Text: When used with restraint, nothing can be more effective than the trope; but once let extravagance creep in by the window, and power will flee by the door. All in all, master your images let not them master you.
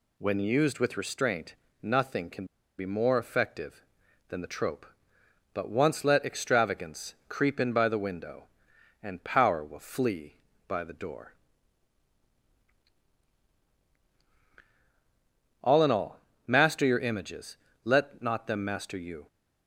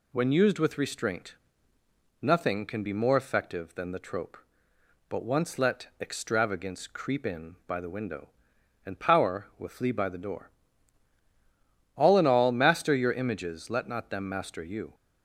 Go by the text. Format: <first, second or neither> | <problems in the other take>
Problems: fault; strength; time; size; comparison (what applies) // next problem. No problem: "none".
second | pauses between "can" and "be"; slight; at 2.4 s; 0.33 s long // pauses between "images" and "let"; slight; at 17.5 s; 0.28 s long